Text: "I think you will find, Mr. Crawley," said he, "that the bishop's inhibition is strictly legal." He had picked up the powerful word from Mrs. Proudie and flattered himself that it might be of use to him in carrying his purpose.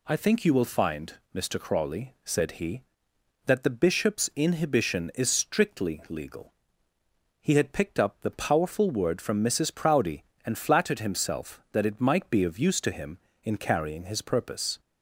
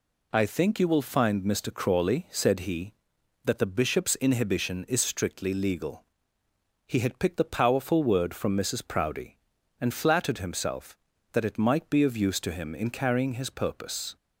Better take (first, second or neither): first